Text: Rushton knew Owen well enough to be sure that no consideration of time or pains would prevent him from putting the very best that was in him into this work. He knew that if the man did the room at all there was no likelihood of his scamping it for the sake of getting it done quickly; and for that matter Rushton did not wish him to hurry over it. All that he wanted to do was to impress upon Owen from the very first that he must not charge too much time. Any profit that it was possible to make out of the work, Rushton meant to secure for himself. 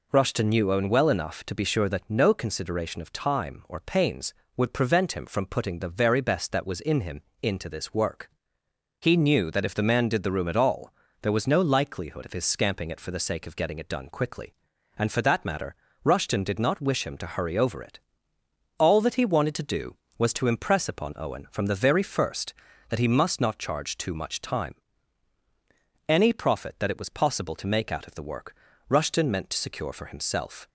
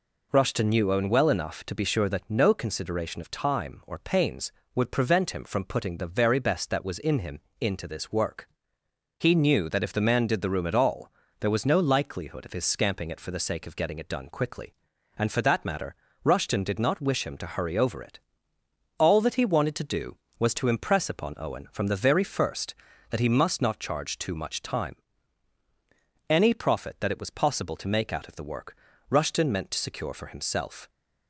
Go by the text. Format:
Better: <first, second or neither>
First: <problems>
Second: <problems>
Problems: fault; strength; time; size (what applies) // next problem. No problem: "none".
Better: neither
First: pauses between "him" and "into"; slight; at 7.2 s; 0.22 s long // pauses between "all" and "there"; slight; at 10.9 s; 0.28 s long // pauses between "matter" and "Rushton"; slight; at 15.7 s; 0.30 s long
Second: pauses between "him" and "into"; slight; at 7.3 s; 0.22 s long // pauses between "all" and "there"; slight; at 11.1 s; 0.28 s long // pauses between "matter" and "Rushton"; slight; at 15.9 s; 0.30 s long